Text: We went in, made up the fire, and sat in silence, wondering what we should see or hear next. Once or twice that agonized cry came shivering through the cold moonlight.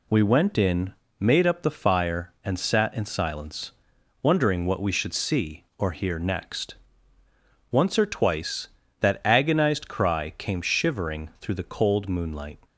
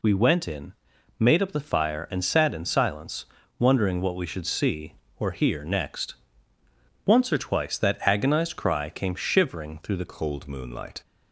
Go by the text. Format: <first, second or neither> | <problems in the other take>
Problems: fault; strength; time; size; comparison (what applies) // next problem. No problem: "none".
first | changes voice at "cold"; from 10.0 s on; 1.0 s long